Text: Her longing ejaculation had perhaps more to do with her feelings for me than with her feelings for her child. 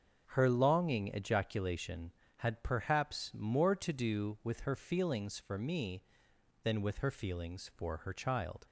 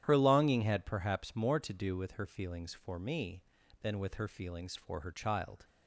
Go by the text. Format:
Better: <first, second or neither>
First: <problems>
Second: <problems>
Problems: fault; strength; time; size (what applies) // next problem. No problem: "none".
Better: first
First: starts louder than the rest; until 1.2 s; 6.5 dB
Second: starts louder than the rest; strong; until 1.0 s; 10.5 dB // skips "ejaculation"; at 0.6 s